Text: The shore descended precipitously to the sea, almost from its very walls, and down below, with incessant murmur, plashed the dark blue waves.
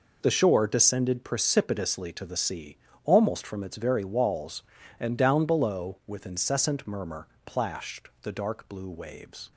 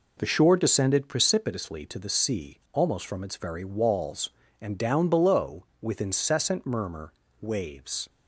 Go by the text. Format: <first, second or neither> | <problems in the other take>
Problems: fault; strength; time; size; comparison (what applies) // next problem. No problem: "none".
first | skips "plashed the dark blue"; at 7.2 s